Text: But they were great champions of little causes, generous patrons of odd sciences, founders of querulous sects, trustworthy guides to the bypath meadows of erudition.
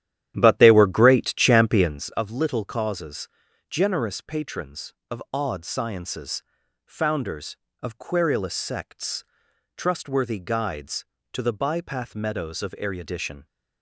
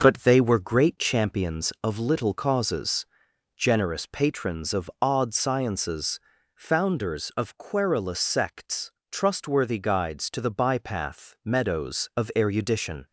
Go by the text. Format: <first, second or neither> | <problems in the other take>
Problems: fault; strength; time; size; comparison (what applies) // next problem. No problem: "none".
second | starts louder than the rest; strong; until 2.1 s; 11 dB